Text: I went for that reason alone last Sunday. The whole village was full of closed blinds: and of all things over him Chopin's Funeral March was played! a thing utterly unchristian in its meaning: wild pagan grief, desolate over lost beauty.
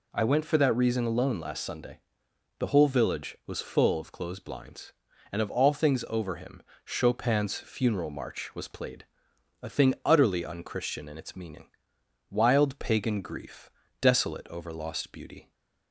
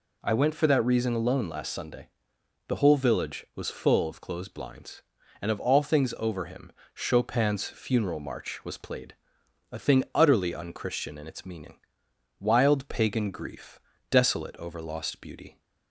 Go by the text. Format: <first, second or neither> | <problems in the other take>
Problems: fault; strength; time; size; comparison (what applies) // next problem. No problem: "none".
neither | pauses between "him" and "Chopin's"; slight; the same in both